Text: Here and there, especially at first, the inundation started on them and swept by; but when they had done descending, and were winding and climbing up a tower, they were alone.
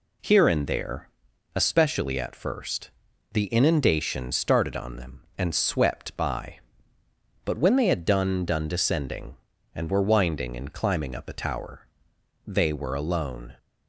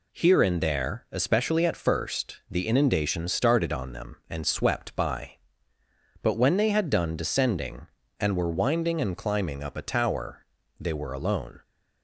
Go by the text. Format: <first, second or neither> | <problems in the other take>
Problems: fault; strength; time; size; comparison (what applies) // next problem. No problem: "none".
second | says "done" twice; at 8.4 s